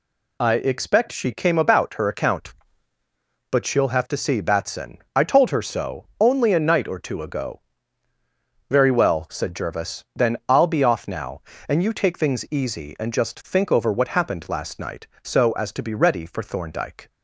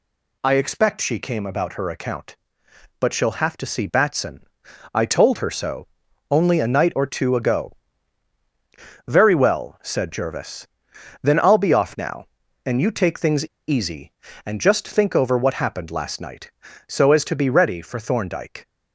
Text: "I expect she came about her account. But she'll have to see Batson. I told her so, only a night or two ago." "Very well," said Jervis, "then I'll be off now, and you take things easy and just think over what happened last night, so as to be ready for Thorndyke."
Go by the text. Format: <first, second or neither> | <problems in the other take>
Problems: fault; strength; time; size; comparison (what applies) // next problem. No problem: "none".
first | pauses between "things" and "easy"; slight; at 13.4 s; 0.23 s long